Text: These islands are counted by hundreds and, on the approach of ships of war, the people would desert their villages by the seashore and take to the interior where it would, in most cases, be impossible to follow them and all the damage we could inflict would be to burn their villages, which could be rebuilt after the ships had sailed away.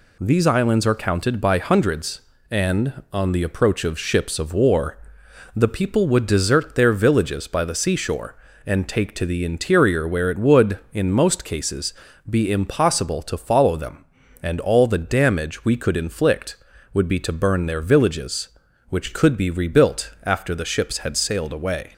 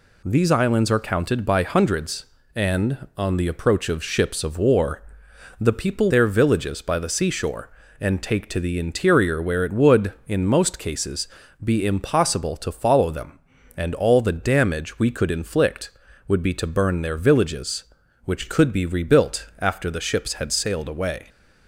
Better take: first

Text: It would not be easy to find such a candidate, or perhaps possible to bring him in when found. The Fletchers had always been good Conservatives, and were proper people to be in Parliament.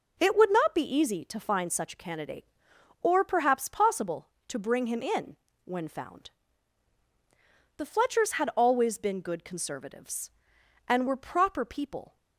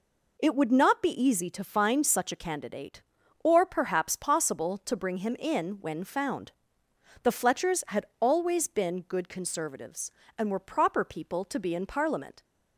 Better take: second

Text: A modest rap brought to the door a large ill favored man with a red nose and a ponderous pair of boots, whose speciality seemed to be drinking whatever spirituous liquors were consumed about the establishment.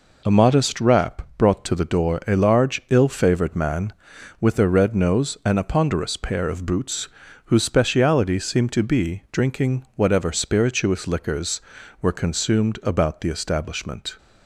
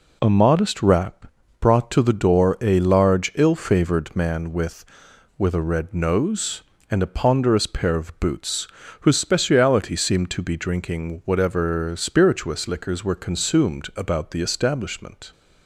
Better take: first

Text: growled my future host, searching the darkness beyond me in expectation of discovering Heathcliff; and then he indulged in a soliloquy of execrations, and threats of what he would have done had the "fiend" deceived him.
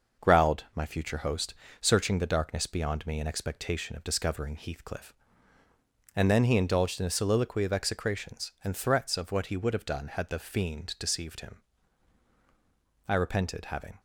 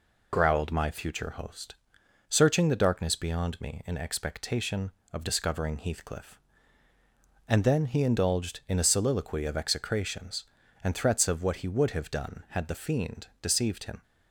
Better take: second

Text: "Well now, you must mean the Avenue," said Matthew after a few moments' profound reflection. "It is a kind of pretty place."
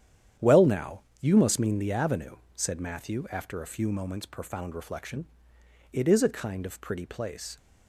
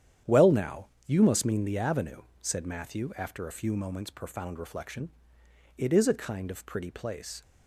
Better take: neither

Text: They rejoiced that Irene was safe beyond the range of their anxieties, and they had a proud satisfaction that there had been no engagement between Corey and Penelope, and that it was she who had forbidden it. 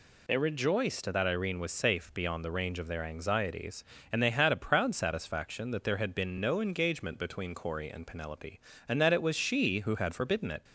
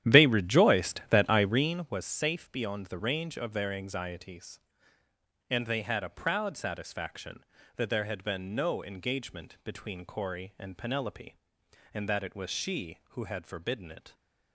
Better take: first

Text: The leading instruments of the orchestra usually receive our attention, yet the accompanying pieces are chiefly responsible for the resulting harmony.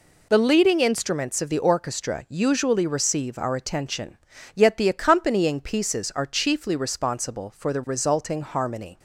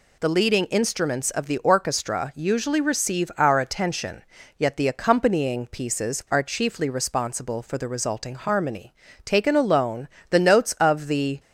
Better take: first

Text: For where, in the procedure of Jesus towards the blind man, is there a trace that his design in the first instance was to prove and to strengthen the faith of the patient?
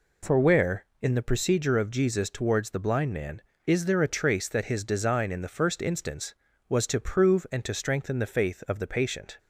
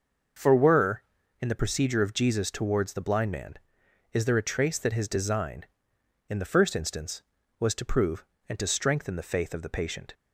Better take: first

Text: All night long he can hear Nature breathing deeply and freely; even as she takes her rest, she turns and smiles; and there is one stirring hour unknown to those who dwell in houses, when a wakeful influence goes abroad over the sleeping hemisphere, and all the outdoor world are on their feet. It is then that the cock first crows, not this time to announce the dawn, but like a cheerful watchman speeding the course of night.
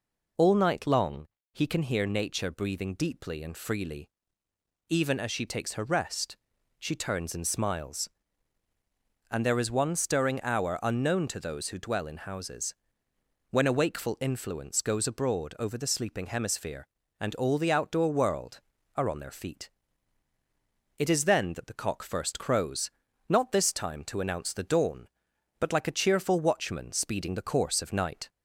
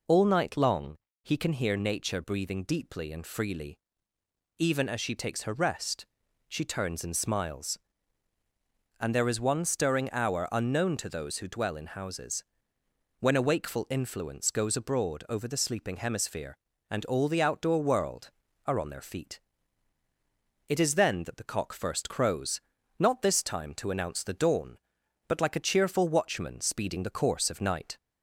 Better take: neither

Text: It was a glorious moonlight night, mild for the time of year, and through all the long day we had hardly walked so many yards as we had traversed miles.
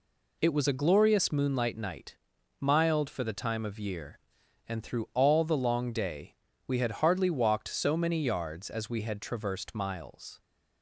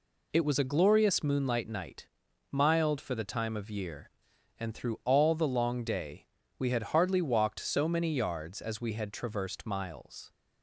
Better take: neither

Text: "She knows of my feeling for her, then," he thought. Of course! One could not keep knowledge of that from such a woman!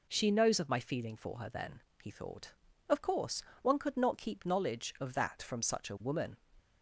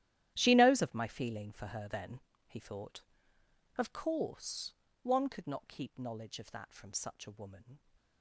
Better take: first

